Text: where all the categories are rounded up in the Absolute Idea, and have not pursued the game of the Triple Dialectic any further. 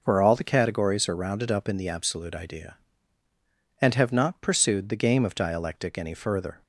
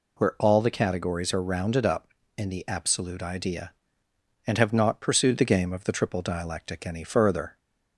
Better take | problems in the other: second | skips "the Triple"; at 5.3 s

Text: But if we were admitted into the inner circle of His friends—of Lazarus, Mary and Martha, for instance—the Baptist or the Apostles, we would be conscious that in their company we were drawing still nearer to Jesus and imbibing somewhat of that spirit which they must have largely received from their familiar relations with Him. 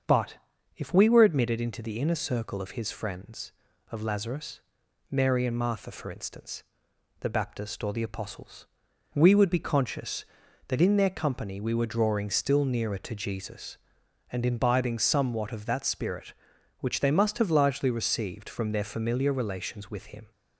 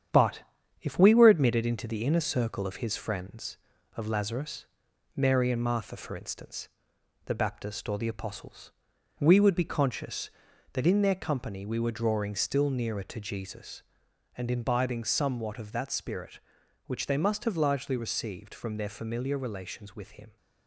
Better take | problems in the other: first | gets quieter; noticeable; throughout; 5 dB // starts louder than the rest; strong; until 1.5 s; 9 dB; also in the first // pauses between "But" and "if"; at 0.4 s; 0.38 s long; also in the first

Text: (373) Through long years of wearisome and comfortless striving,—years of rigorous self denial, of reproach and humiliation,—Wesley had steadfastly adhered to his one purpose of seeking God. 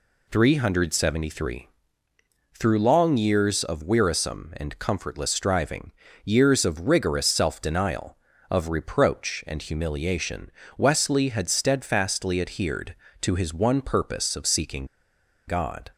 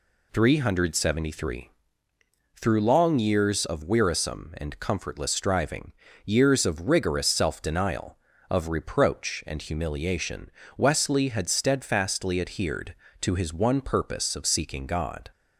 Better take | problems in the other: second | pauses between "seeking" and "God"; noticeable; at 14.8 s; 0.62 s long

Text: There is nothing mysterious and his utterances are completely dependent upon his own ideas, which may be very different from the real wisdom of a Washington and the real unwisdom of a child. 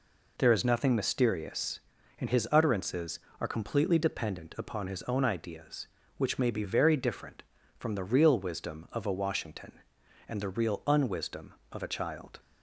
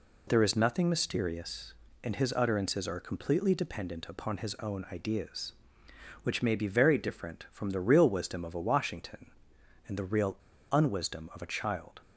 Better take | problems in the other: first | pauses between "real" and "unwisdom"; slight; at 10.3 s; 0.34 s long

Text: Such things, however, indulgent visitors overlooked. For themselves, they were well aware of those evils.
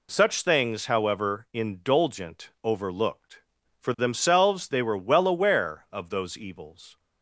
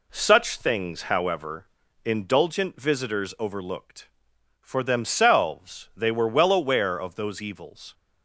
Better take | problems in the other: second | skips "visitors"; at 2.5 s

